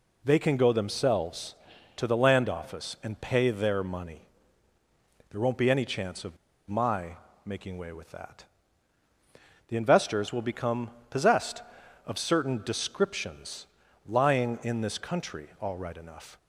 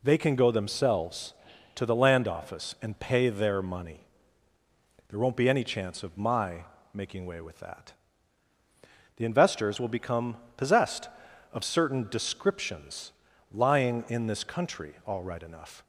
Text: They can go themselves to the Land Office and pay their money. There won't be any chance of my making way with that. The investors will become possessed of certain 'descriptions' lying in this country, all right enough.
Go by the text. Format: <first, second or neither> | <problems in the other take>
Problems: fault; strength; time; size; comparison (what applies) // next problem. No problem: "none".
second | pauses between "of" and "my"; slight; at 6.3 s; 0.32 s long // pauses between "my" and "making"; slight; at 7.1 s; 0.28 s long; slight in the second // pauses between "become" and "possessed"; slight; at 10.8 s; 0.20 s long; slight in the second // pauses between "descriptions" and "lying"; at 13.6 s; 0.40 s long; also in the second